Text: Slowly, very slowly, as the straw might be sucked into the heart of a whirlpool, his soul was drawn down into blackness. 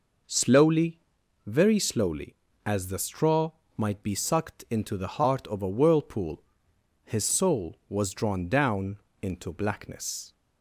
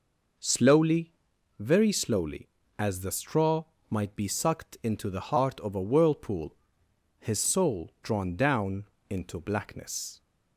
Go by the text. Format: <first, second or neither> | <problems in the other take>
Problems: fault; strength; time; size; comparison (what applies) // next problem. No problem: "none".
first | pauses between "straw" and "might"; slight; at 3.6 s; 0.24 s long; slight in the first // skips "was"; at 7.9 s // pauses between "down" and "into"; slight; at 8.8 s; 0.22 s long; slight in the first